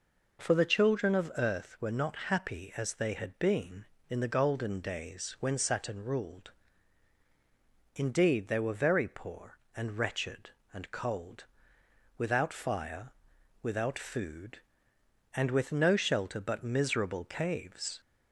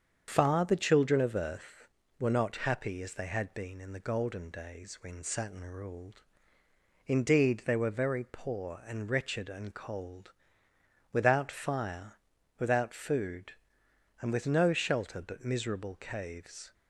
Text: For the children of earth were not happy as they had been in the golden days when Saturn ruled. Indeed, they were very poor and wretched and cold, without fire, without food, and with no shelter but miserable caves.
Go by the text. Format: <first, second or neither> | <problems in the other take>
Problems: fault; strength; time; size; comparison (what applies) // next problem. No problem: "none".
first | starts louder than the rest; strong; until 1.3 s; 7.5 dB // says "Far" for "For"; at 0.3 s